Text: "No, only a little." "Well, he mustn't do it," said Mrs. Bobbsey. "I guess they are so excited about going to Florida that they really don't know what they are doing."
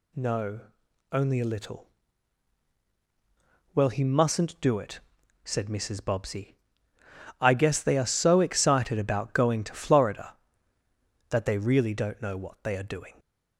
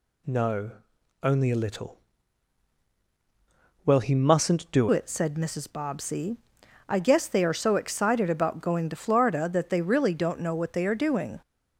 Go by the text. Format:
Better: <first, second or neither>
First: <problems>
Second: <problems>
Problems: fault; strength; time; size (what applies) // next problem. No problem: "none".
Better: first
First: none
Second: changes voice at "it"; from 4.9 s on; 6.5 s long